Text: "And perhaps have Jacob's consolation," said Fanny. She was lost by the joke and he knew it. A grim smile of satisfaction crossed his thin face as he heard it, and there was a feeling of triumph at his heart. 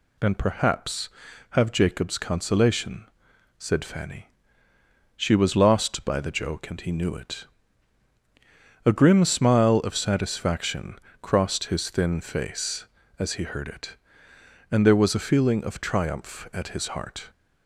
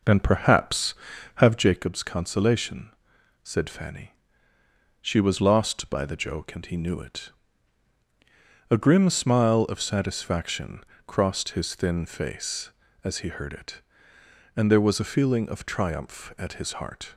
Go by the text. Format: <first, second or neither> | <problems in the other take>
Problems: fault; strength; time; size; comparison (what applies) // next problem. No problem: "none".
first | starts louder than the rest; noticeable; until 1.8 s; 5 dB // pauses between "satisfaction" and "crossed"; slight; at 10.8 s; 0.24 s long; slight in the first